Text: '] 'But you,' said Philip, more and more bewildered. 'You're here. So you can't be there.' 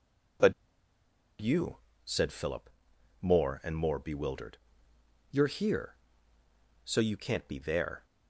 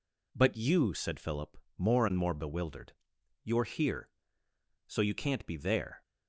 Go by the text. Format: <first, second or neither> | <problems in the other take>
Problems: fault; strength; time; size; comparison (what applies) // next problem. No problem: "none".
second | pauses between "But" and "you"; noticeable; at 0.5 s; 0.87 s long